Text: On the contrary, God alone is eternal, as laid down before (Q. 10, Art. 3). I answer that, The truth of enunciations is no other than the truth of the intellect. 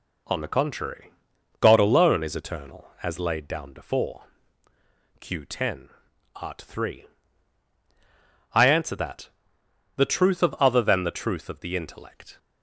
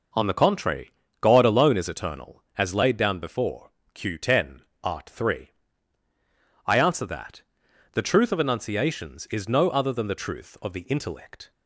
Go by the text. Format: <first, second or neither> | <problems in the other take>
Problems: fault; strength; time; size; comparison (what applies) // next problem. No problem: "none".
second | skips "enunciations is no"; at 10.5 s